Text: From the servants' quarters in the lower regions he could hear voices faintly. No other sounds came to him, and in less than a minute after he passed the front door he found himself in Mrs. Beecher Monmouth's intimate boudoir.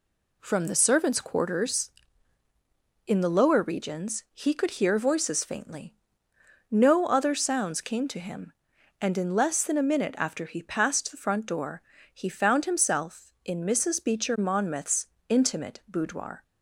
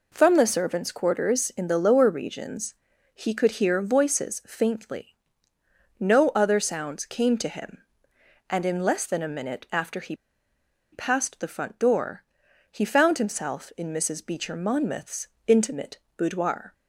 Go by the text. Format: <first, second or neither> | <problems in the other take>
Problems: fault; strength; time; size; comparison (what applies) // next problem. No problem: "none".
first | pauses between "regions" and "he"; at 2.7 s; 0.40 s long // pauses between "he" and "passed"; noticeable; at 10.1 s; 0.77 s long // pauses between "door" and "he"; noticeable; at 12.2 s; 0.48 s long; slight in the first // pauses between "Monmouth's" and "intimate"; slight; at 15.2 s; 0.20 s long; slight in the first // pauses between "intimate" and "boudoir"; slight; at 15.9 s; 0.18 s long